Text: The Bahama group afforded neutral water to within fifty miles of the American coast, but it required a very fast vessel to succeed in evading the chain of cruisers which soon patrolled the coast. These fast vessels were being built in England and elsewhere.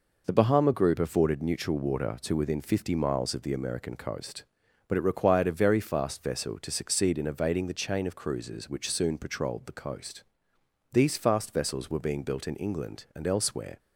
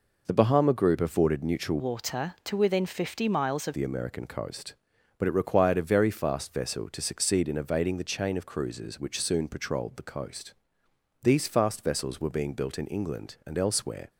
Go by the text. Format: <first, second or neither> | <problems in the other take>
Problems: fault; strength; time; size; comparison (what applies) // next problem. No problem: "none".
first | changes voice from "water" to "of"; from 1.7 to 3.7 s; 2.0 s long